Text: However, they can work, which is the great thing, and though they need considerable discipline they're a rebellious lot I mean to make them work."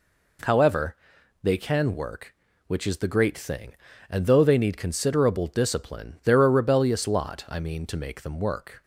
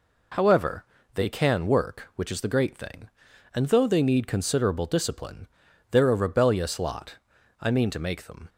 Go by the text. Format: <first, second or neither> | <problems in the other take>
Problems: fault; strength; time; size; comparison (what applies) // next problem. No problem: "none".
first | pauses between "discipline" and "they're"; at 5.4 s; 0.44 s long // pauses between "lot" and "I"; at 7.1 s; 0.44 s long // stops before "work"; at 8.4 s